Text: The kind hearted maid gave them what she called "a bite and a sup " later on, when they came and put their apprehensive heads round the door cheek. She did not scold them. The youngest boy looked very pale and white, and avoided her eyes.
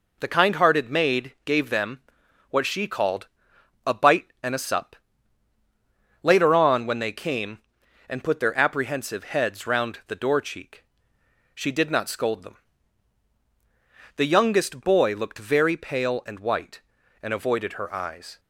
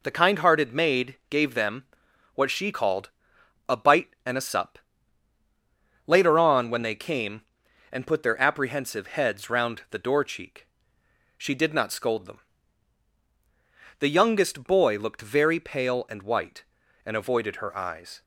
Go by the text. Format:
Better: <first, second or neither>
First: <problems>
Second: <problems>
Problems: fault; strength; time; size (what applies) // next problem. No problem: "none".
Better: neither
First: pauses between "them" and "what"; noticeable; at 2.0 s; 0.50 s long // pauses between "called" and "a"; noticeable; at 3.2 s; 0.60 s long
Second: pauses between "them" and "what"; noticeable; at 1.8 s; 0.50 s long // pauses between "called" and "a"; noticeable; at 3.0 s; 0.60 s long